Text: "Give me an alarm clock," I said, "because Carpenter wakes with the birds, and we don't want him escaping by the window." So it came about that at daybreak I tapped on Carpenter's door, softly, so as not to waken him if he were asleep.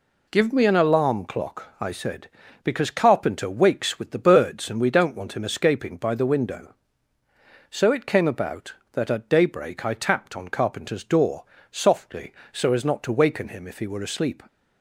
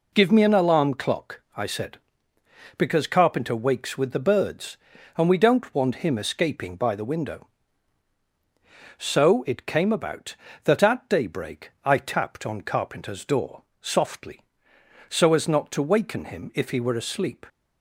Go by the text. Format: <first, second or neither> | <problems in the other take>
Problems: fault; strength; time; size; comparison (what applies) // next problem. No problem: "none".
neither | none